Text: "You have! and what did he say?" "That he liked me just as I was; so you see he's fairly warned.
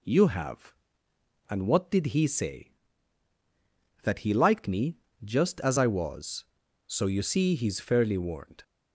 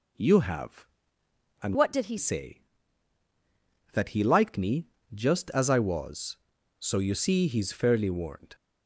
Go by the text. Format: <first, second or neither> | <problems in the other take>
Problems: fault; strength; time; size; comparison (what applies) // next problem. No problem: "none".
first | changes voice from "what" to "he"; from 1.7 to 2.1 s; 0.4 s long // pauses between "me" and "just"; slight; at 4.8 s; 0.26 s long; slight in the first